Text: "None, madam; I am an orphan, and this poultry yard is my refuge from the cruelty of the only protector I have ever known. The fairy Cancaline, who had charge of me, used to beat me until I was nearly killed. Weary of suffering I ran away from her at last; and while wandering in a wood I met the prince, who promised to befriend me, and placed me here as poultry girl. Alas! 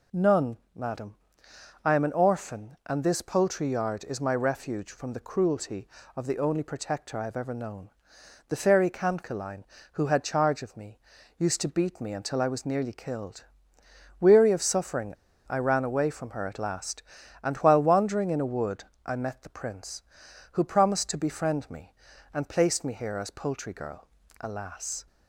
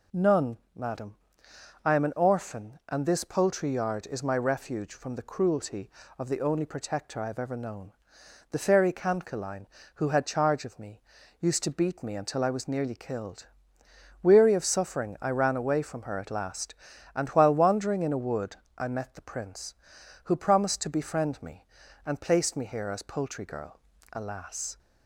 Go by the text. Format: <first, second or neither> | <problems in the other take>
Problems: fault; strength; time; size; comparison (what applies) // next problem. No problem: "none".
second | pauses between "suffering" and "I"; slight; at 15.1 s; 0.34 s long // pauses between "wood" and "I"; slight; at 18.8 s; 0.22 s long; slight in the second